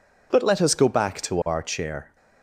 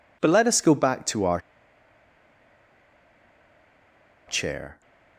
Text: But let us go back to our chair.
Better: first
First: none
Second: pauses between "our" and "chair"; strong; at 1.4 s; 2.8 s long

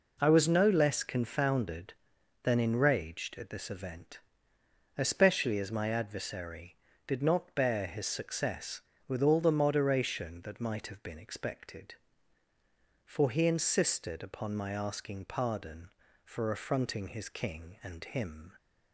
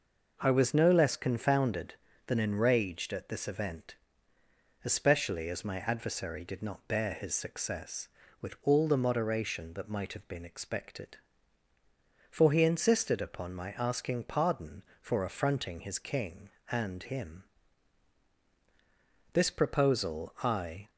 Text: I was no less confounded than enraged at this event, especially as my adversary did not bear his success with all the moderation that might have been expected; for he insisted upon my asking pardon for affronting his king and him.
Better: first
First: none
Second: goes on to say "This proposal I"; from 19.3 s on; 1.5 s long

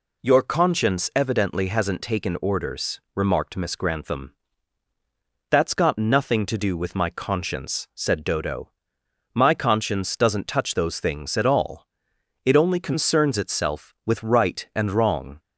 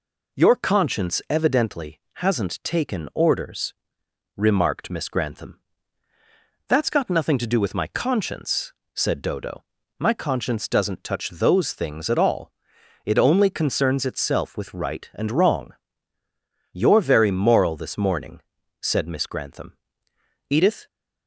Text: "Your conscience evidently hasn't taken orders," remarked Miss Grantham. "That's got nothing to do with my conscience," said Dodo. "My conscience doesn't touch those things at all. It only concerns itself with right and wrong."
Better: first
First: none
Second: goes on to say "You're very moral this morning said Miss Grantham Edith"; strong; from 16.7 s on; 4.1 s long

